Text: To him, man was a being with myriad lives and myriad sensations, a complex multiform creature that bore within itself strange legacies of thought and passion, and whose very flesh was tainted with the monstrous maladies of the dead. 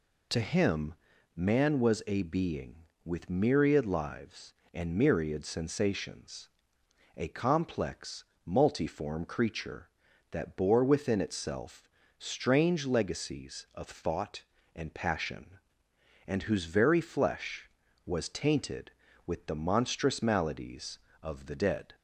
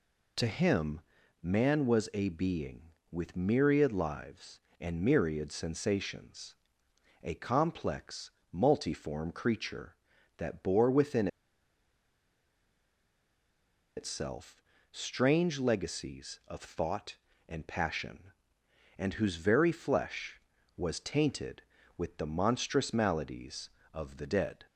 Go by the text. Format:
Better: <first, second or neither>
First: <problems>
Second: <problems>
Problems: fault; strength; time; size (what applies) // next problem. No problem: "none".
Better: first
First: pauses between "complex" and "multiform"; slight; at 8.2 s; 0.20 s long // pauses between "itself" and "strange"; slight; at 11.8 s; 0.30 s long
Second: pauses between "complex" and "multiform"; slight; at 8.3 s; 0.20 s long // pauses between "within" and "itself"; strong; at 11.2 s; 2.6 s long // pauses between "itself" and "strange"; slight; at 14.6 s; 0.30 s long